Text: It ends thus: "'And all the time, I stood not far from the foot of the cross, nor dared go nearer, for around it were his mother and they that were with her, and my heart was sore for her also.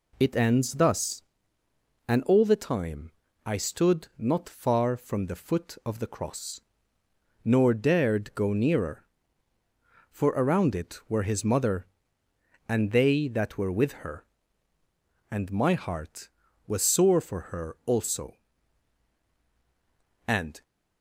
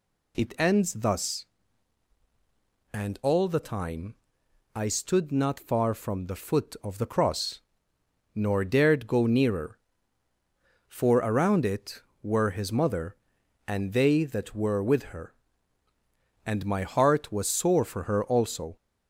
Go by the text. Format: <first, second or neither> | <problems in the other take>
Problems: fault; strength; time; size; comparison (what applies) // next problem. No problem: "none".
second | goes on to say "And"; slight; from 20.2 s on; 0.36 s long